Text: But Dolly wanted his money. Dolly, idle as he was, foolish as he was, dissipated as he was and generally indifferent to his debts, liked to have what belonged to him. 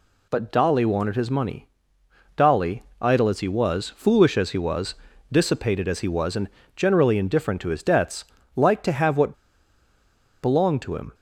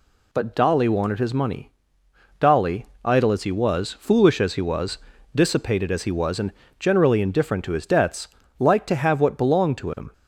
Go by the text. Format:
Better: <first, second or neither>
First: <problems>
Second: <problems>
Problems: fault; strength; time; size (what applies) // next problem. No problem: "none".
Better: second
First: pauses between "and" and "generally"; slight; at 6.4 s; 0.26 s long // pauses between "what" and "belonged"; at 9.3 s; 1.0 s long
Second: pauses between "and" and "generally"; slight; at 6.5 s; 0.26 s long